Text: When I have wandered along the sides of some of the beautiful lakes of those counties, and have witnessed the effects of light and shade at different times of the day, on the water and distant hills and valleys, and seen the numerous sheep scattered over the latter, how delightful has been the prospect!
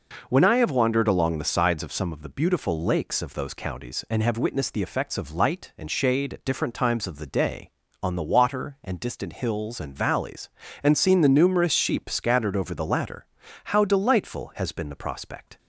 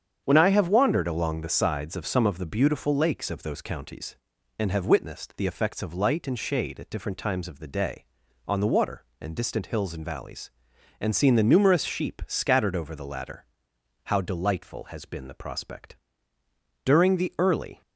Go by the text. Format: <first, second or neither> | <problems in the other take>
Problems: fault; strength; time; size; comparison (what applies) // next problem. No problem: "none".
first | starts louder than the rest; strong; until 1.2 s; 8 dB // goes on to say "During the early"; noticeable; from 16.8 s on; 0.96 s long